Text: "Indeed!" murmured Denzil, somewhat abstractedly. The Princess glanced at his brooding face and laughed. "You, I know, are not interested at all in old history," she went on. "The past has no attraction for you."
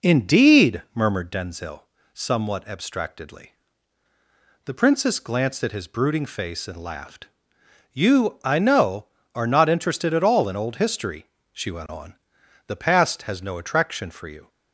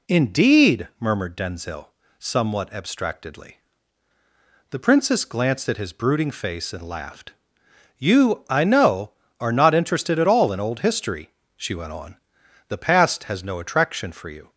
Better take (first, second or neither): second